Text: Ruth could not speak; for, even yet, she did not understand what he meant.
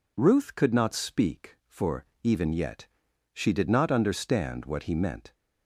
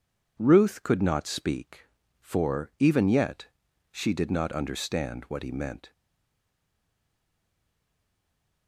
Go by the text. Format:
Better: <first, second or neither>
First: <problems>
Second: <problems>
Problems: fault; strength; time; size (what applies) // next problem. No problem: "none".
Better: first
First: none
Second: stays silent after the last word; strong; from 5.9 s on; 2.7 s long